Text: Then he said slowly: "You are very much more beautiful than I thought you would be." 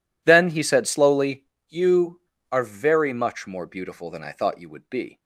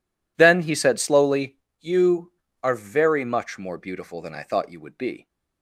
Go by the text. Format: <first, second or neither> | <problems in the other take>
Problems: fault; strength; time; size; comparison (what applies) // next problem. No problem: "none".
neither | none